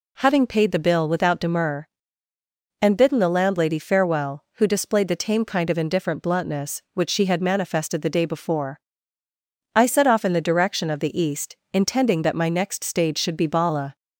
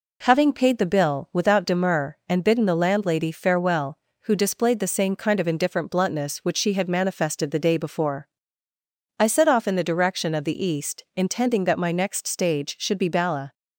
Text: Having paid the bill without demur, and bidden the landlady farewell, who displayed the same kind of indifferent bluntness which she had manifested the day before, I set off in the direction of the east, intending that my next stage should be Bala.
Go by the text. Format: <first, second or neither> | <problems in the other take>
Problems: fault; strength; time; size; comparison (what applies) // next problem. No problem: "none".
second | says "tame" for "same"; at 5.1 s